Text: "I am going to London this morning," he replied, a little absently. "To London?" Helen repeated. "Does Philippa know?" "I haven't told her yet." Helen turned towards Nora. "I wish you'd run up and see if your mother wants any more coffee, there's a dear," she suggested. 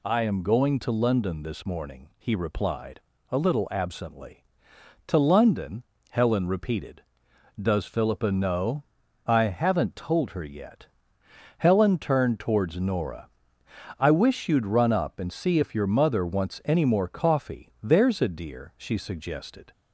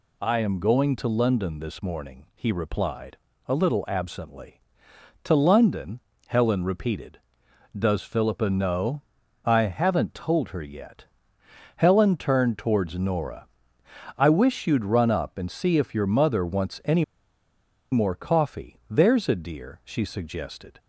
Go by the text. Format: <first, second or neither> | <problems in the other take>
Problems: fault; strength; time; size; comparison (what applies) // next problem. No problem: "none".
first | pauses between "any" and "more"; noticeable; at 17.0 s; 0.88 s long